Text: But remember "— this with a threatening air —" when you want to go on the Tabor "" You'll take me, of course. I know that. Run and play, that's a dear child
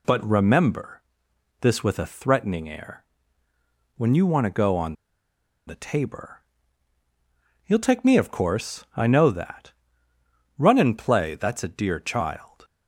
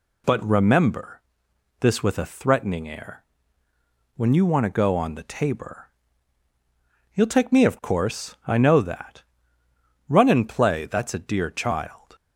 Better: second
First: pauses between "on" and "the"; noticeable; at 4.9 s; 0.73 s long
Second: none

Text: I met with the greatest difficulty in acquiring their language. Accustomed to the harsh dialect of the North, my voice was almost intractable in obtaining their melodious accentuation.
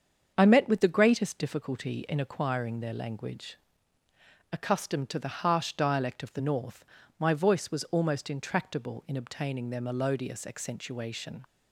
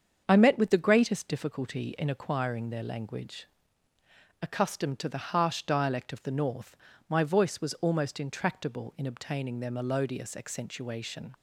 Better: neither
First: starts louder than the rest; strong; until 1.3 s; 7 dB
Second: starts louder than the rest; strong; until 1.2 s; 7 dB

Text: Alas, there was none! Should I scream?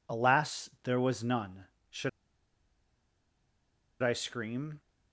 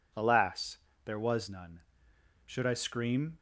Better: second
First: pauses between "Should" and "I"; strong; at 2.0 s; 1.9 s long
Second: none

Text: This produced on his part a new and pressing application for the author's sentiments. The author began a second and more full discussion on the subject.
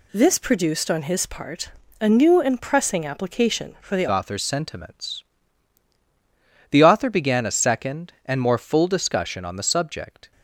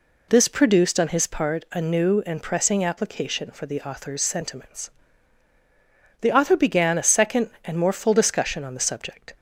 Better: second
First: pauses between "part" and "a"; slight; at 1.6 s; 0.32 s long // changes voice at "author's"; from 4.0 s on; 6.3 s long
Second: none

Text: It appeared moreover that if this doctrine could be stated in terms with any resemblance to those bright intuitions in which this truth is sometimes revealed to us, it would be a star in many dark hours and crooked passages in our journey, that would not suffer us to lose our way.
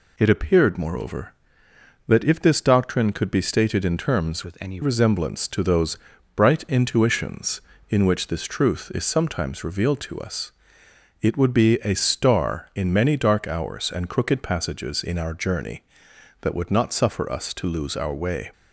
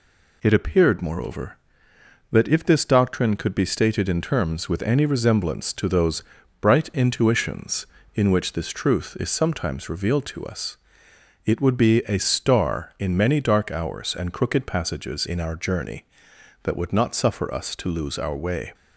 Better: second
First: changes voice from "with" to "any"; from 4.4 to 4.8 s; 0.4 s long // pauses between "those" and "bright"; at 5.9 s; 0.38 s long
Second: pauses between "those" and "bright"; at 6.2 s; 0.38 s long

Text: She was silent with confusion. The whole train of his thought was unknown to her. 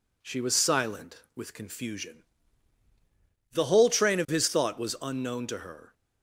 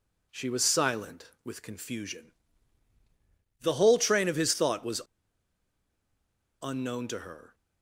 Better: first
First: none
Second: pauses between "was" and "unknown"; strong; at 5.0 s; 1.6 s long

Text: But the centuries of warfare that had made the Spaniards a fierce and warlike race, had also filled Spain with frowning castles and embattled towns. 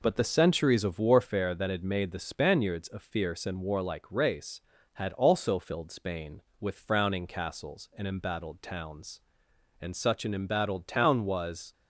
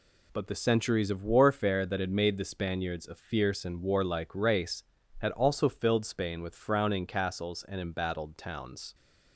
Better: second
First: goes on to say "And such an embattled town was"; strong; from 9.7 s on; 1.9 s long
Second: none

